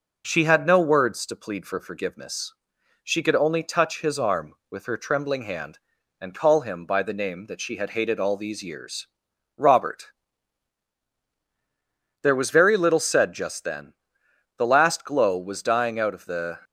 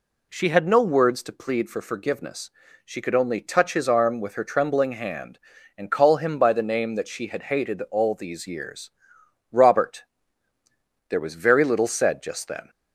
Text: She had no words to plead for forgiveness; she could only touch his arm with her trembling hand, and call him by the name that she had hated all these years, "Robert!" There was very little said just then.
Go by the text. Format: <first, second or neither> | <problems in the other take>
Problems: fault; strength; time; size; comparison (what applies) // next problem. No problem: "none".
second | goes on to say "The last glow was dying out of the"; strong; from 14.5 s on; 2.0 s long